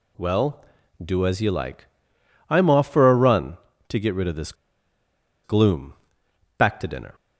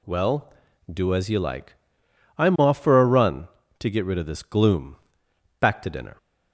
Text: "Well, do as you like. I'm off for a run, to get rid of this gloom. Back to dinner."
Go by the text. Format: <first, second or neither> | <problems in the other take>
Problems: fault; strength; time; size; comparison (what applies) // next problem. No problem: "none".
second | pauses between "this" and "gloom"; noticeable; at 4.5 s; 0.91 s long